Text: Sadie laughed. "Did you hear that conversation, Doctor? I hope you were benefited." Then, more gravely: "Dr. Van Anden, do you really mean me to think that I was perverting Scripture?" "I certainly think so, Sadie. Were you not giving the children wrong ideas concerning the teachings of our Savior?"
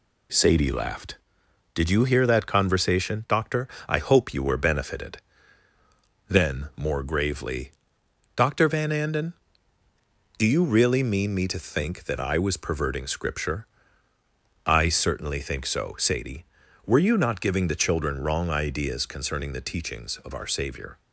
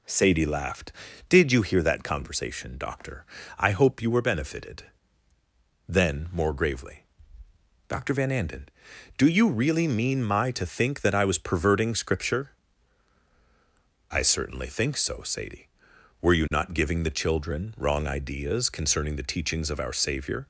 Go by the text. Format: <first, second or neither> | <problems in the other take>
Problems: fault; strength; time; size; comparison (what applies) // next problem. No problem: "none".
first | says "my" for "me"; at 10.2 s